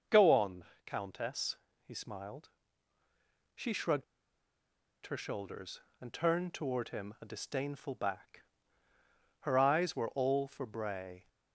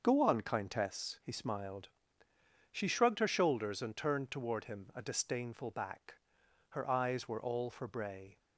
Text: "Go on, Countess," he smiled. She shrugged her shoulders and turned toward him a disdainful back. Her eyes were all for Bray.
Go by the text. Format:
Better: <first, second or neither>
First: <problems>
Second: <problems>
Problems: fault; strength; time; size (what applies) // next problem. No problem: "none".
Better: second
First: starts louder than the rest; until 1.3 s; 6 dB // pauses between "shrugged" and "her"; at 4.0 s; 1.0 s long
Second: starts louder than the rest; until 1.0 s; 6 dB